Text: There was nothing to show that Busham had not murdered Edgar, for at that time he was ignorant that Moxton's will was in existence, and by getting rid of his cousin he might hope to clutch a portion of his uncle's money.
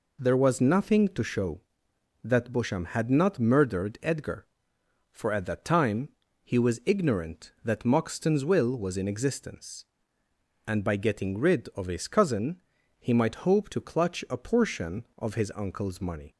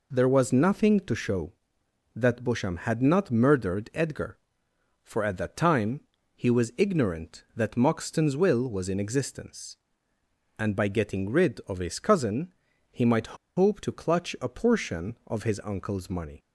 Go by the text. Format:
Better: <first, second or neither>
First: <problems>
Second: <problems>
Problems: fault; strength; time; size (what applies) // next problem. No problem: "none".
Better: first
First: pauses between "time" and "he"; slight; at 6.0 s; 0.34 s long // pauses between "cousin" and "he"; at 12.5 s; 0.42 s long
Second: pauses between "time" and "he"; slight; at 6.0 s; 0.34 s long // pauses between "cousin" and "he"; at 12.4 s; 0.42 s long // pauses between "might" and "hope"; slight; at 13.3 s; 0.22 s long